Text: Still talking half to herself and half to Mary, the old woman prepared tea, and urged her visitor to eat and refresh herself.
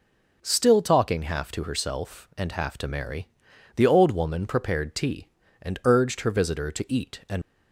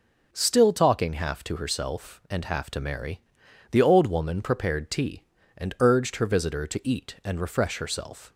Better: second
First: stops before "refresh herself"; at 7.4 s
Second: none

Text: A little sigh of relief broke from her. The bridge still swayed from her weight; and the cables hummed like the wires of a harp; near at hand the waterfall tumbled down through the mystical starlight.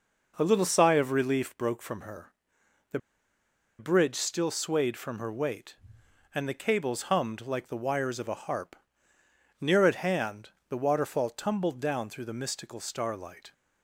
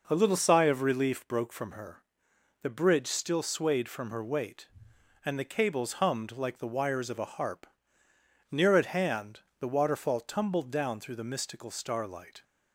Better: second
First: pauses between "The" and "bridge"; noticeable; at 2.9 s; 0.81 s long // pauses between "hand" and "the"; slight; at 10.5 s; 0.18 s long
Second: pauses between "hand" and "the"; slight; at 9.4 s; 0.18 s long

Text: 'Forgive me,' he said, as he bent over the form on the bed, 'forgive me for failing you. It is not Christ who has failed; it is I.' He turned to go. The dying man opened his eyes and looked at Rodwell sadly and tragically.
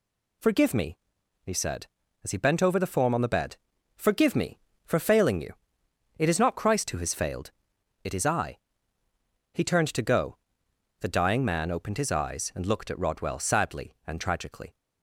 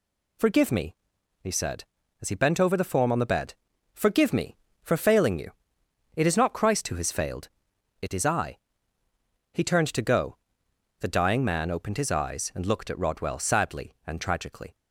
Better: neither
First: none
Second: none

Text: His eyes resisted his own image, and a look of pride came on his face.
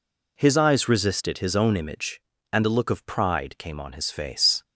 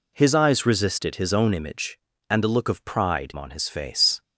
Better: first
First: none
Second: skips "came"; at 3.3 s

